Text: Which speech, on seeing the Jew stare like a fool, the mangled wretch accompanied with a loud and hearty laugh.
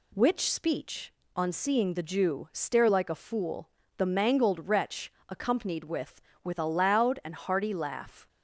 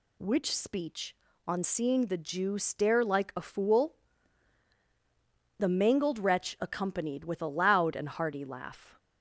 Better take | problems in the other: second | pauses between "wretch" and "accompanied"; slight; at 5.1 s; 0.20 s long // says "with" twice; at 6.4 s

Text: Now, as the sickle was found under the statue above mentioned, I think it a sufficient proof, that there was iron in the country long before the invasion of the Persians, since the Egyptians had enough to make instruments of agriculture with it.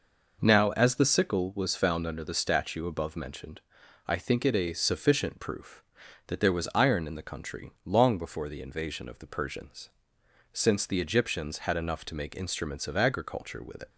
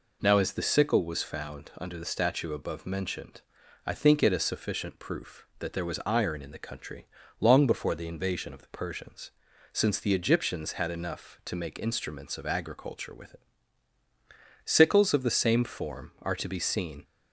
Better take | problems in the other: first | pauses between "country" and "long"; slight; at 7.0 s; 0.34 s long // goes on to say "Sickles of the same form are to be seen"; strong; from 14.6 s on; 2.3 s long

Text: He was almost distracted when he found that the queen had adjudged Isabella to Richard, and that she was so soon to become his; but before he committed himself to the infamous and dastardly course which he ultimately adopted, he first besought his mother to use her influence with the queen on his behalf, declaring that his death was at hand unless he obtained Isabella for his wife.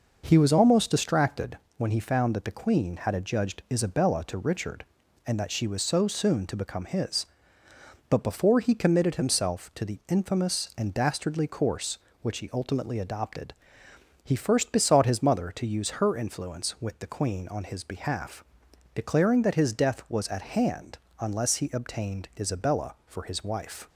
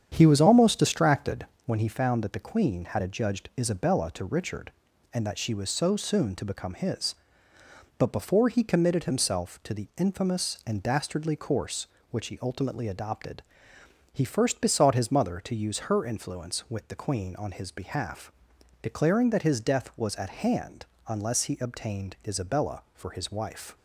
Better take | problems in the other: first | starts louder than the rest; strong; until 1.9 s; 8.5 dB // pauses between "distracted" and "when"; slight; at 1.4 s; 0.18 s long; slight in the first // pauses between "hand" and "unless"; slight; at 20.8 s; 0.20 s long; slight in the first

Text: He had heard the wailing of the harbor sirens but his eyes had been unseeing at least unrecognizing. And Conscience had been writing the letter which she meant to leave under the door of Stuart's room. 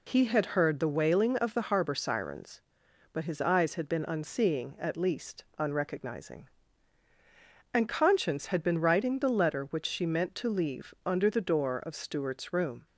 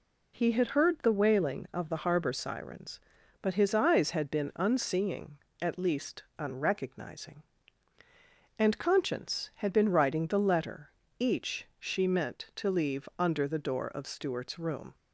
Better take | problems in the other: first | pauses between "least" and "unrecognizing"; slight; at 6.2 s; 0.16 s long // says "each" for "which"; at 11.2 s

